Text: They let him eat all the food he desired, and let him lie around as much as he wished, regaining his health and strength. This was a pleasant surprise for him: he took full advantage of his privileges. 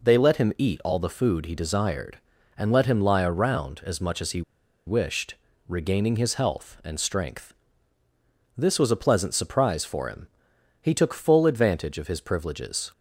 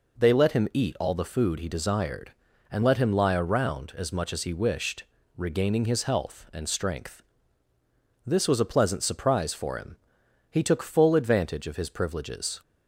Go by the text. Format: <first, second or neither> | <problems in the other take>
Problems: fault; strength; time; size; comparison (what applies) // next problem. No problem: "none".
second | pauses between "he" and "wished"; at 4.4 s; 0.45 s long